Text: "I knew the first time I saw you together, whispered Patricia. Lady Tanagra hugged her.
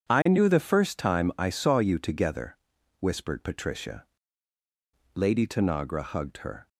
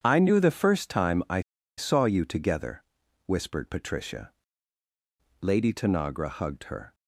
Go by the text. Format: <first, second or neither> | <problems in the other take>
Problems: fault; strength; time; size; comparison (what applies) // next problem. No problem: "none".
first | pauses between "I" and "saw"; at 1.4 s; 0.36 s long